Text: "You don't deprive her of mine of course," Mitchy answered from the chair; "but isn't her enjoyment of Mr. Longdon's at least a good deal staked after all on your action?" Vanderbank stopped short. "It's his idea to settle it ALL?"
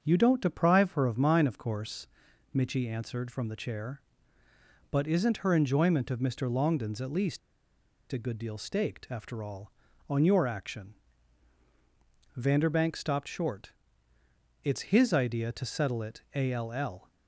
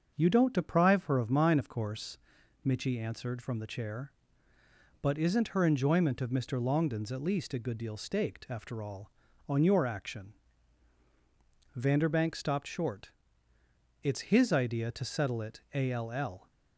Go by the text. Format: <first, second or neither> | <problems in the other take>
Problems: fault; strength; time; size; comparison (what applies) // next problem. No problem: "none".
second | starts louder than the rest; until 1.0 s; 6.5 dB; also in the second // pauses between "least" and "a"; noticeable; at 7.3 s; 0.73 s long // pauses between "it" and "ALL"; slight; at 16.2 s; 0.16 s long; slight in the second